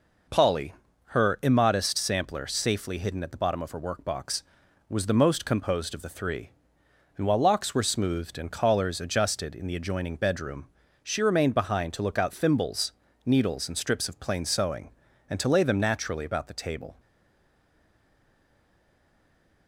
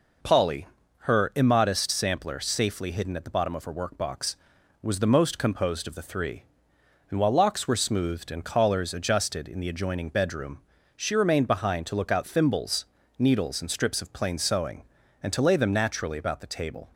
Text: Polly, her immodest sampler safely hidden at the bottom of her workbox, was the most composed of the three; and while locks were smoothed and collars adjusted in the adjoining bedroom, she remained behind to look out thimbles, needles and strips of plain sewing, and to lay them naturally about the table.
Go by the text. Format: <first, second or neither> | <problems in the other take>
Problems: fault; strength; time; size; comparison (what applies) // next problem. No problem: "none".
second | stays silent after the last word; strong; from 16.9 s on; 2.7 s long